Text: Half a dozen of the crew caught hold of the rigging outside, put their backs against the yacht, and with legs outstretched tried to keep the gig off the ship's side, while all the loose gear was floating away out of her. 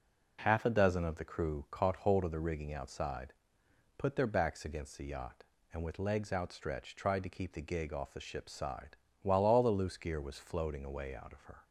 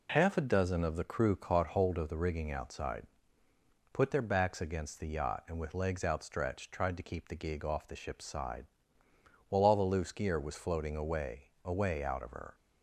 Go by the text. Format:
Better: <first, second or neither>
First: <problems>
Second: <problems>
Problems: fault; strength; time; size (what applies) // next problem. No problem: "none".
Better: first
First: none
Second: says "away" twice; at 11.6 s